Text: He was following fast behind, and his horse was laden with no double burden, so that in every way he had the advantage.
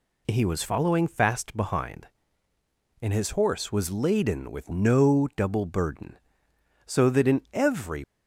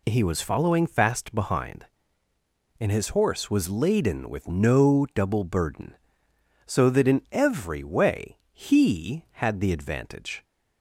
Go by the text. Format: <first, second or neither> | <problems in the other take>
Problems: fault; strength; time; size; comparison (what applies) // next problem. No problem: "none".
second | stops before "way he had the advantage"; at 8.0 s